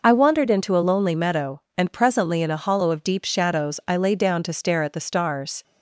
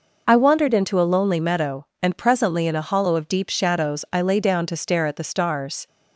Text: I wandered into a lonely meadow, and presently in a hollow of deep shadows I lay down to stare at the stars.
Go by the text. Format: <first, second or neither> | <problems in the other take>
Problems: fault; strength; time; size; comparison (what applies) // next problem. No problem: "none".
neither | none